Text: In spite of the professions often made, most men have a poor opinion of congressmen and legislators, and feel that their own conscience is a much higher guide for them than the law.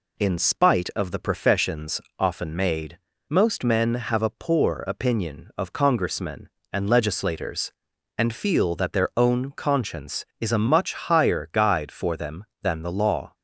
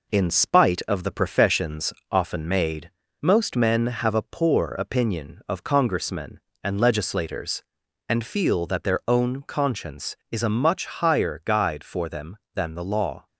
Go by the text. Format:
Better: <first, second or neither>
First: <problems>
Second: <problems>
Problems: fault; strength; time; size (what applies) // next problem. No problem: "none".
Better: first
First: pauses between "professions" and "often"; slight; at 1.9 s; 0.18 s long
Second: gets quieter; slight; throughout; 2.5 dB // pauses between "professions" and "often"; slight; at 1.9 s; 0.18 s long